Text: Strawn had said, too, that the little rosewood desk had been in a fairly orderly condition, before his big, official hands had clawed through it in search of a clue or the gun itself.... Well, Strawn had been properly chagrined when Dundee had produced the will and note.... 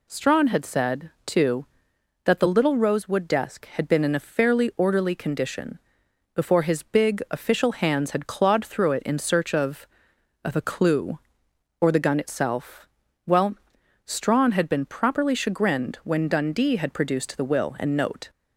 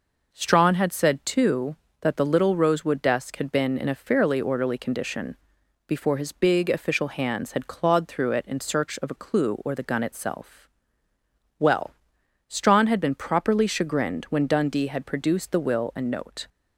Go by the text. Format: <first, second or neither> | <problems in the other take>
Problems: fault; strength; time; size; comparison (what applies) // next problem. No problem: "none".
second | says "of" twice; at 10.4 s